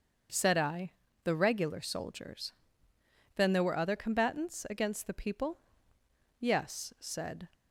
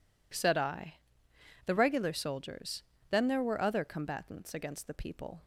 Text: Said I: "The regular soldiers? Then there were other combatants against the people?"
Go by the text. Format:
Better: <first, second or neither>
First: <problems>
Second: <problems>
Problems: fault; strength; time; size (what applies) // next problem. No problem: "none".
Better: second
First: starts louder than the rest; until 1.6 s; 6.5 dB // goes on to say "Yes said"; noticeable; from 6.3 s on; 1.1 s long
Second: none